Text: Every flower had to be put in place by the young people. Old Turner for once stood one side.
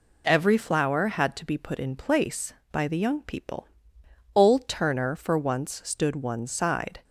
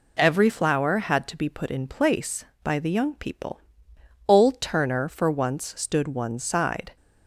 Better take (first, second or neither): neither